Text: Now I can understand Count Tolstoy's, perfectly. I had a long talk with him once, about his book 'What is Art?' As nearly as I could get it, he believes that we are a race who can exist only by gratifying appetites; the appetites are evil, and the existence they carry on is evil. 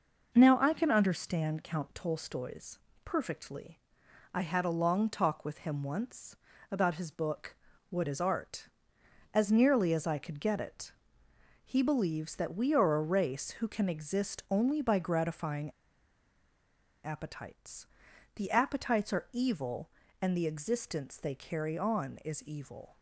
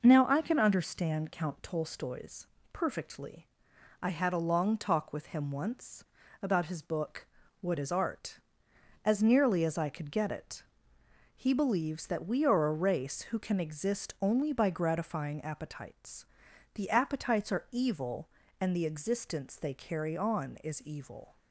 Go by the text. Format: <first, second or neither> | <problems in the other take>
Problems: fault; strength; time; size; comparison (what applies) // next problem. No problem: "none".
second | pauses between "book" and "What"; slight; at 7.5 s; 0.36 s long; slight in the second // pauses between "gratifying" and "appetites"; strong; at 15.6 s; 1.3 s long